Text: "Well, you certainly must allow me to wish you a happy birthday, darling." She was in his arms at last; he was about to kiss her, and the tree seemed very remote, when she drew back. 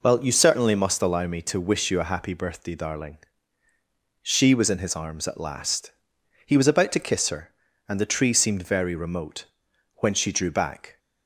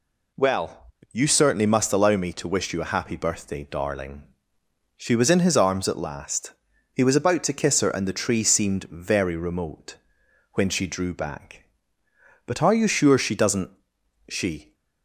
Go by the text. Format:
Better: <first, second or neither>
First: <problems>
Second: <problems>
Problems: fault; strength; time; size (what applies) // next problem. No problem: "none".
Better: first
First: none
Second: goes on to say "But are you sure she doesn't she"; strong; from 12.4 s on; 2.2 s long